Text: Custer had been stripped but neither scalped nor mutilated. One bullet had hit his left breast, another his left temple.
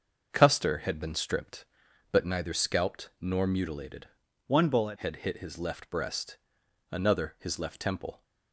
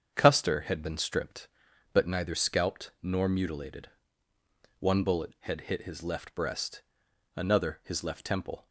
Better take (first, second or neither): second